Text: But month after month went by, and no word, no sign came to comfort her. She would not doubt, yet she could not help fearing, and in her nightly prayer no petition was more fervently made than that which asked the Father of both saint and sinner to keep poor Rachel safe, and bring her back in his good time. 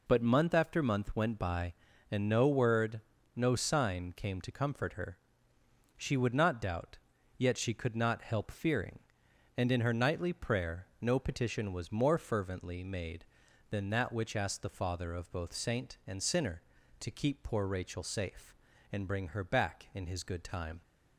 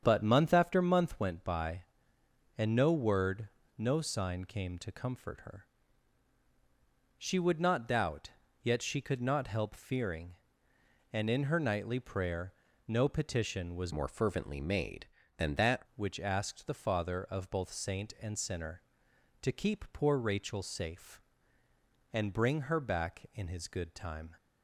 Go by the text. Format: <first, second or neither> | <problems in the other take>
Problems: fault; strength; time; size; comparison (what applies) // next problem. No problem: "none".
first | starts louder than the rest; strong; until 1.0 s; 7.5 dB // pauses between "prayer" and "no"; slight; at 12.5 s; 0.34 s long // changes voice from "more" to "that"; from 13.9 to 15.8 s; 1.9 s long